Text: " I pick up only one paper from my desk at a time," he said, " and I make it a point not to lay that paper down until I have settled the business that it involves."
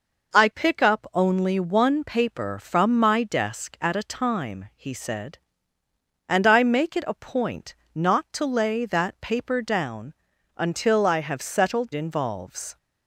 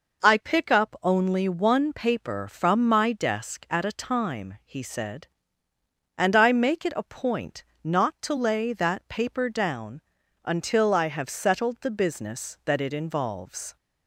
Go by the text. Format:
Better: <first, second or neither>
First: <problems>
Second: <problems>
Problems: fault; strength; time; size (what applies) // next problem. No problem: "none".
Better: second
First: pauses between "point" and "not"; slight; at 7.7 s; 0.20 s long // pauses between "down" and "until"; at 10.1 s; 0.42 s long // skips "the business that it"; at 11.9 s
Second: pauses between "point" and "not"; slight; at 7.6 s; 0.20 s long // pauses between "down" and "until"; at 10.0 s; 0.42 s long